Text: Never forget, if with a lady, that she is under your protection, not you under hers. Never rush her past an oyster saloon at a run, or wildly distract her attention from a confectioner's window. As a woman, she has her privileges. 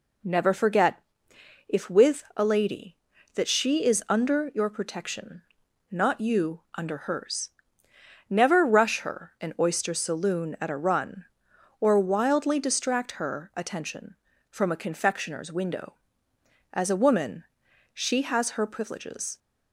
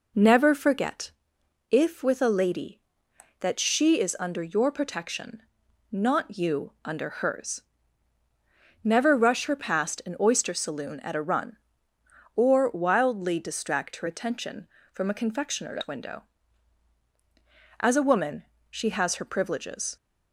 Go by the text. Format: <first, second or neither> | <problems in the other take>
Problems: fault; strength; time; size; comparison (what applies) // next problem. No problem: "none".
second | skips "past"; at 9.3 s